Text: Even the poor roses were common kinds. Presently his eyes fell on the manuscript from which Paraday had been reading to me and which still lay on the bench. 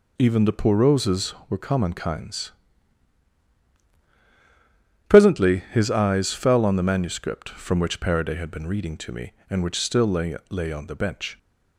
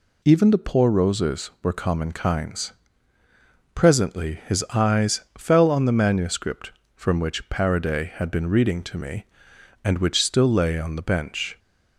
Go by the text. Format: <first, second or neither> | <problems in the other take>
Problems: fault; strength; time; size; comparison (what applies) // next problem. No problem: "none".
second | says "lay" twice; at 10.4 s